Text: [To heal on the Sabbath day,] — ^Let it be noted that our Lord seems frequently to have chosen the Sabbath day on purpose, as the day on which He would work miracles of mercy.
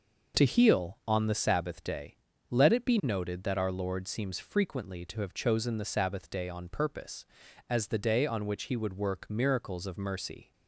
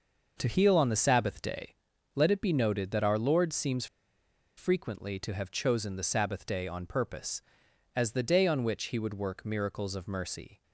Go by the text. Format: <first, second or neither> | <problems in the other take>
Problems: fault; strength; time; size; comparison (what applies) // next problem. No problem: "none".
first | pauses between "seems" and "frequently"; noticeable; at 3.8 s; 0.71 s long